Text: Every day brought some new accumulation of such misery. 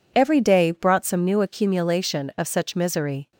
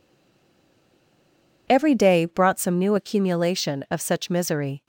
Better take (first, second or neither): first